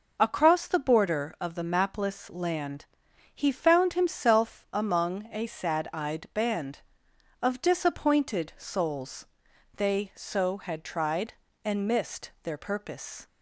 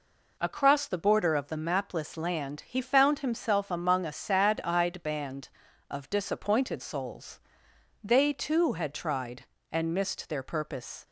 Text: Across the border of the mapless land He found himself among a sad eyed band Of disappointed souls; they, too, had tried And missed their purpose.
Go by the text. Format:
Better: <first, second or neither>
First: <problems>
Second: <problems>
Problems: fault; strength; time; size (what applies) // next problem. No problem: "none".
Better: second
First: pauses between "land" and "He"; noticeable; at 2.8 s; 0.48 s long // says "so" for "too"; at 10.1 s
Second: none